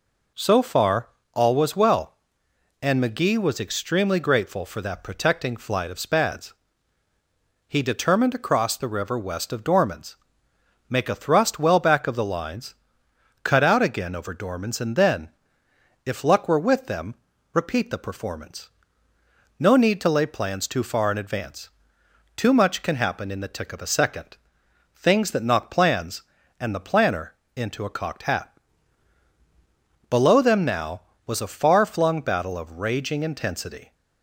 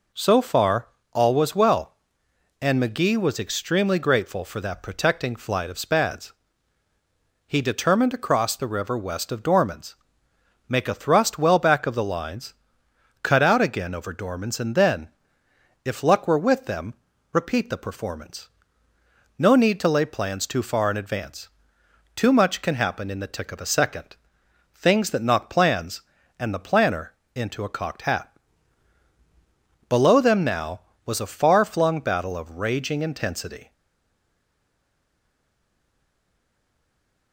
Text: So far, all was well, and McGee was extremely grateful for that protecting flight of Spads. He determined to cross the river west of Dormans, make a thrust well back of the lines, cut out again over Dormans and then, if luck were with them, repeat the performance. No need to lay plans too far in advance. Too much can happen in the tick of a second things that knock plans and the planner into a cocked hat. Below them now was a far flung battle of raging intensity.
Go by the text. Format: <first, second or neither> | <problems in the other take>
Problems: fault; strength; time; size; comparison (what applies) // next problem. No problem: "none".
first | pauses between "second" and "things"; noticeable; at 24.1 s; 0.58 s long; noticeable in the first // pauses between "planner" and "into"; slight; at 27.1 s; 0.24 s long; slight in the first // stays silent after the last word; strong; from 33.7 s on; 3.6 s long